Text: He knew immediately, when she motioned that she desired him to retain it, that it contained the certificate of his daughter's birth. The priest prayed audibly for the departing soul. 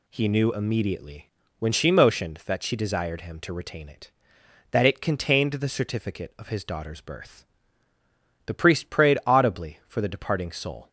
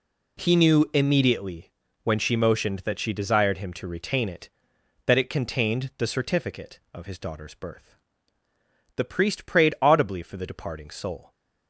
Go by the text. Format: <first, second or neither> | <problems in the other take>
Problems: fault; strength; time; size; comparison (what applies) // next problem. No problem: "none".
neither | none